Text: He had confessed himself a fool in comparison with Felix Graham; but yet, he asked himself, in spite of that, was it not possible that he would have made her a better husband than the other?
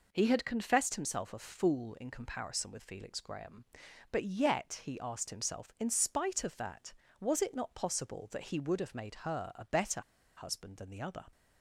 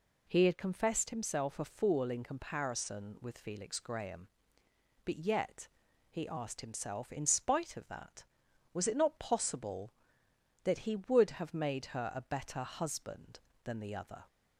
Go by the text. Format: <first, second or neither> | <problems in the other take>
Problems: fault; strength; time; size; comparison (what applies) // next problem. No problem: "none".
second | pauses between "better" and "husband"; at 10.0 s; 0.36 s long